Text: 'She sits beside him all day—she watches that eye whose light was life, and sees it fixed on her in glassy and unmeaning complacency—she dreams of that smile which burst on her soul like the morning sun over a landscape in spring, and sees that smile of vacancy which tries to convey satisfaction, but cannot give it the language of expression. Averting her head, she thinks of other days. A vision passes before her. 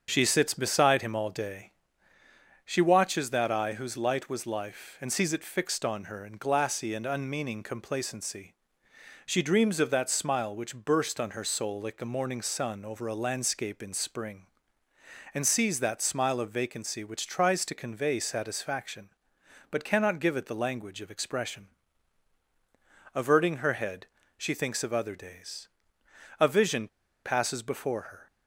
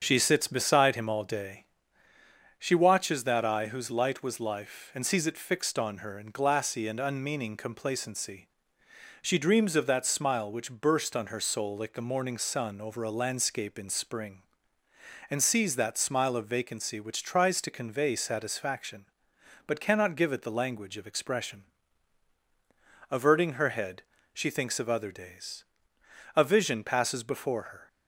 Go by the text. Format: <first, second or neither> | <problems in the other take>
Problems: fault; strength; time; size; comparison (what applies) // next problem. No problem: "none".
second | starts louder than the rest; strong; until 1.1 s; 7 dB; strong in the second // pauses between "vision" and "passes"; at 26.8 s; 0.37 s long